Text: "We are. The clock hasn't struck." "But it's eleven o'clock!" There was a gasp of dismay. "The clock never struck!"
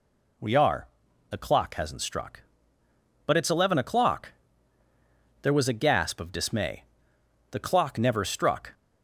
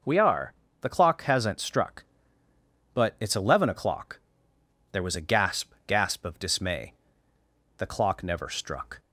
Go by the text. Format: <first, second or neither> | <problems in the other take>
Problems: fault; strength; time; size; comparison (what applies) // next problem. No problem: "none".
first | says "gasp" twice; at 5.8 s